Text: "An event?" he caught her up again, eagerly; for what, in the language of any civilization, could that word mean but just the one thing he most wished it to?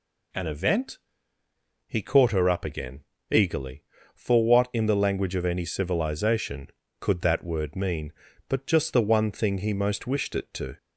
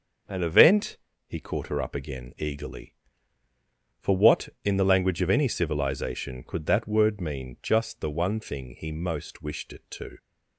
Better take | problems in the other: first | starts louder than the rest; noticeable; until 1.5 s; 6 dB // skips "but"; at 7.5 s

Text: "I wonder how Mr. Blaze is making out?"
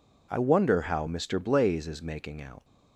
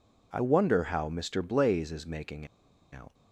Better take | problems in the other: first | pauses between "making" and "out"; at 2.4 s; 0.45 s long

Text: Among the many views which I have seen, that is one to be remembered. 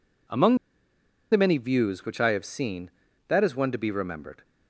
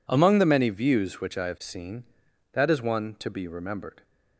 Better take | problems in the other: second | pauses between "Among" and "the"; noticeable; at 0.5 s; 0.74 s long

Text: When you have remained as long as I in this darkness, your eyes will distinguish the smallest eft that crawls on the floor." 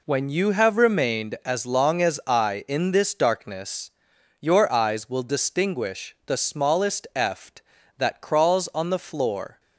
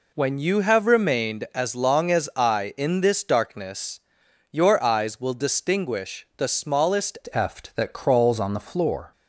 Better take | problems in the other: first | changes voice at "eft"; from 7.3 s on; 1.8 s long

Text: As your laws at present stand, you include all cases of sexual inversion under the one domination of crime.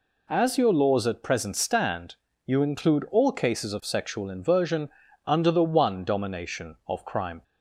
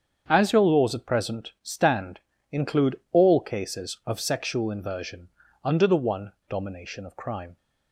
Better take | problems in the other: first | starts louder than the rest; strong; until 1.2 s; 7.5 dB // skips "you"; at 2.3 s // pauses between "inversion" and "under"; slight; at 5.2 s; 0.34 s long; slight in the first // pauses between "one" and "domination"; slight; at 6.3 s; 0.15 s long

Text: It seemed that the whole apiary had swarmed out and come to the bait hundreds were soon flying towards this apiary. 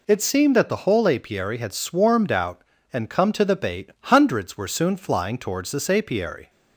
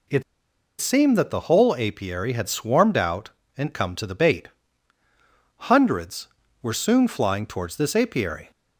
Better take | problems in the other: first | pauses between "It" and "seemed"; noticeable; at 0.2 s; 0.57 s long // pauses between "bait" and "hundreds"; at 4.4 s; 1.2 s long

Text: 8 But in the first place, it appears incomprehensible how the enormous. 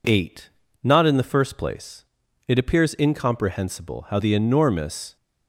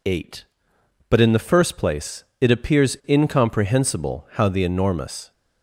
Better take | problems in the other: second | says "Not" for "But"; at 0.8 s

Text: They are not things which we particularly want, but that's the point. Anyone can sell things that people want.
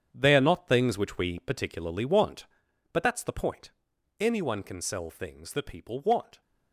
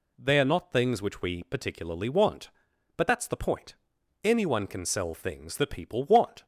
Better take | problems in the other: second | gets quieter; strong; throughout; 11 dB

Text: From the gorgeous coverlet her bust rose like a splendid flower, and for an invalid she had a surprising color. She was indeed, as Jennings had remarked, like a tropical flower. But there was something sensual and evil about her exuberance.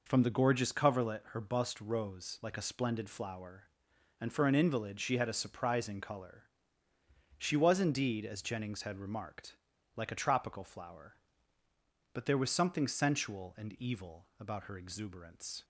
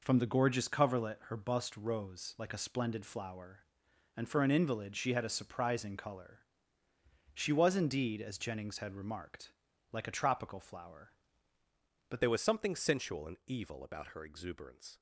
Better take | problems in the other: first | changes voice at "there"; from 12.2 s on; 2.7 s long

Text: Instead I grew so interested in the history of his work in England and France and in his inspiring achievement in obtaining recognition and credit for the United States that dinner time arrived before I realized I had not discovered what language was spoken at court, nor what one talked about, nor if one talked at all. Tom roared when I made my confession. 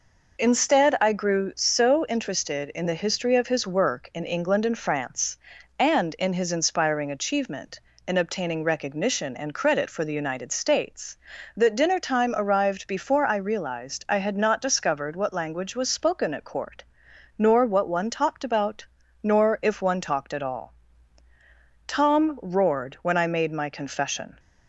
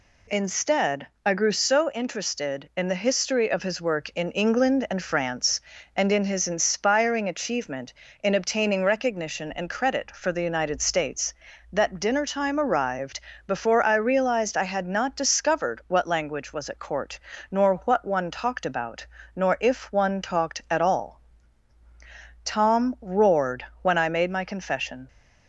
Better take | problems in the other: first | pauses between "Instead" and "I"; slight; at 1.0 s; 0.18 s long // pauses between "arrived" and "before"; slight; at 13.2 s; 0.26 s long // skips "spoken"; at 16.6 s // pauses between "roared" and "when"; slight; at 23.6 s; 0.18 s long

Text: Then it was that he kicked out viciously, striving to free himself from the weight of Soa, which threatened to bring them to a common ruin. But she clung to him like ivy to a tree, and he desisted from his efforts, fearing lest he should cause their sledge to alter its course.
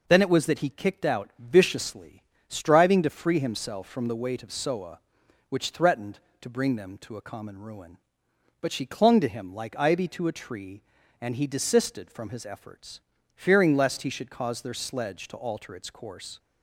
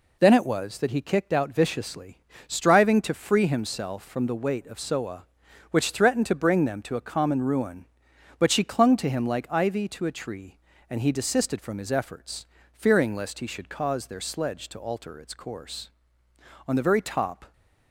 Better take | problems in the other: first | goes on to say "On the very top"; noticeable; from 16.6 s on; 0.86 s long

